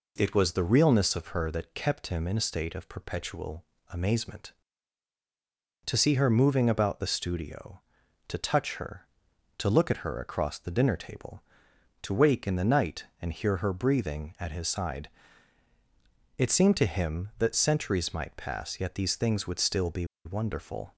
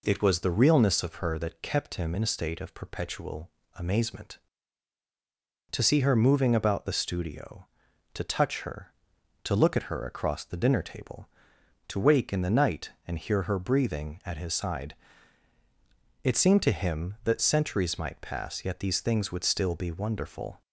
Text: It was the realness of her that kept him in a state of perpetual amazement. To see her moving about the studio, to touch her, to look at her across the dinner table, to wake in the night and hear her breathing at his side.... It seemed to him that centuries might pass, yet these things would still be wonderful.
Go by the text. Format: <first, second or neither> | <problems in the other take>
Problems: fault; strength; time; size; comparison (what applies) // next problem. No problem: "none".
second | pauses between "perpetual" and "amazement"; slight; at 3.6 s; 0.26 s long; slight in the second // pauses between "be" and "wonderful"; slight; at 20.0 s; 0.20 s long